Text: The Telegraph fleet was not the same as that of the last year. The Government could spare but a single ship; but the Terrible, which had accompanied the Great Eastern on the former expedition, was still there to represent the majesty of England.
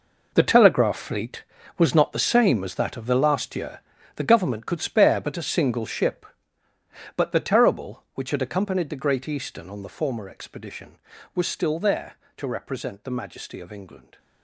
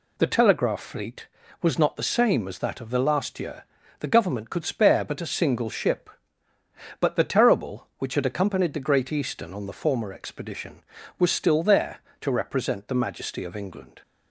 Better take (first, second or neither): second